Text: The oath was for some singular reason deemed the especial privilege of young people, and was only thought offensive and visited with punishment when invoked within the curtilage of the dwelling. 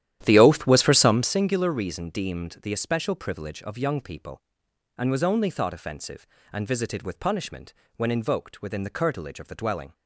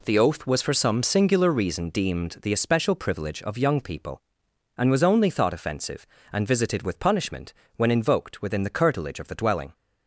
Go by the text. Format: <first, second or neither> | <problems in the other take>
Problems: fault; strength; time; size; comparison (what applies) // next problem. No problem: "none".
second | starts louder than the rest; strong; until 1.4 s; 11.5 dB // pauses between "punishment" and "when"; slight; at 7.7 s; 0.22 s long; slight in the second